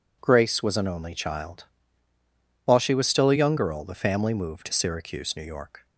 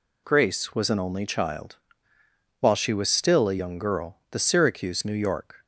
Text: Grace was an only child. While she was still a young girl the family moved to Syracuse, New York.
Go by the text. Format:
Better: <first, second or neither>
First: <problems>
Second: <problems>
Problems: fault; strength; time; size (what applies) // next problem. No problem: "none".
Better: first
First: none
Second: skips "family moved to"; at 4.3 s